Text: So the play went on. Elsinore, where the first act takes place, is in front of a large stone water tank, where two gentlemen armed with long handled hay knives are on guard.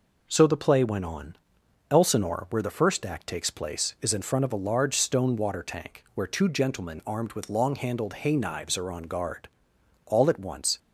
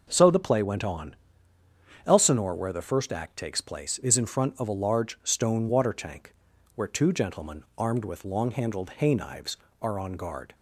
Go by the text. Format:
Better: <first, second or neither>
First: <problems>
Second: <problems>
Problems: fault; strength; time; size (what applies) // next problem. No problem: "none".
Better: second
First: goes on to say "All at once"; noticeable; from 10.0 s on; 0.72 s long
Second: none